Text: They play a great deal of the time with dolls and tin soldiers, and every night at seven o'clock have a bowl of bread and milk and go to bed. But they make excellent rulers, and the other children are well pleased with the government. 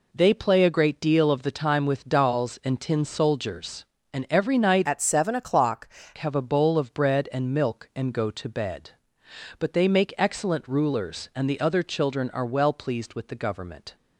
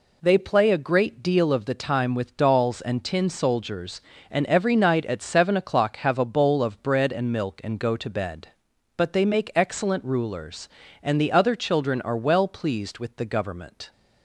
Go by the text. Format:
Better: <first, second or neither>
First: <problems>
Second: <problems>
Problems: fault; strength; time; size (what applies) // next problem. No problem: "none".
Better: second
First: changes voice from "at" to "o'clock"; from 4.8 to 5.8 s; 1.0 s long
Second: none